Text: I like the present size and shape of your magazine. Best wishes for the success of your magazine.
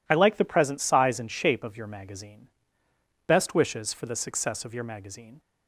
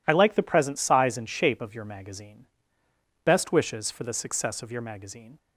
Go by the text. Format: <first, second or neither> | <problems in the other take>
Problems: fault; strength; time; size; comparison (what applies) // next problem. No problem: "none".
neither | none